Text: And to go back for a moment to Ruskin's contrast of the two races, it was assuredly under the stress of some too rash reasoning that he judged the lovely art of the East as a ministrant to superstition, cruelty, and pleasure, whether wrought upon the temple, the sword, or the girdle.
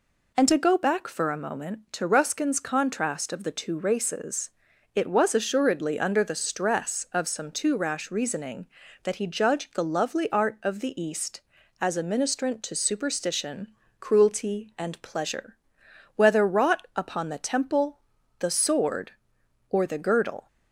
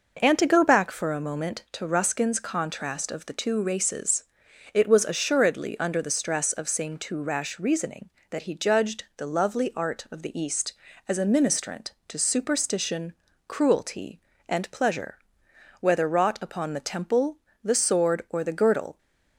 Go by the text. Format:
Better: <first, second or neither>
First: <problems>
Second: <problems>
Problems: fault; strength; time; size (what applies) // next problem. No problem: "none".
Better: first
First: none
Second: says "same" for "some"; at 6.6 s